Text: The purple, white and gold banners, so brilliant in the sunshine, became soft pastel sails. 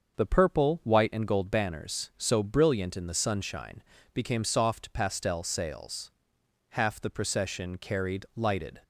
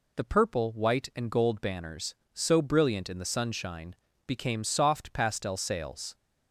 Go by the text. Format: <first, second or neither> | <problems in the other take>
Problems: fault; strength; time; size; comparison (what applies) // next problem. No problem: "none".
second | starts louder than the rest; until 1.2 s; 6.5 dB // goes on to say "Half the procession carried lighted"; strong; from 6.7 s on; 2.1 s long